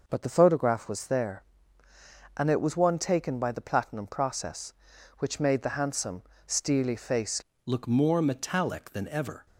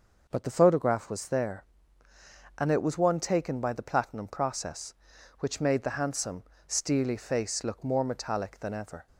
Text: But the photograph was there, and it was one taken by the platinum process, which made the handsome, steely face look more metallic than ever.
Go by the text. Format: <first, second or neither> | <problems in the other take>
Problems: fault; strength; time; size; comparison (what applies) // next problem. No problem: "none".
second | changes voice at "look"; from 7.6 s on; 1.8 s long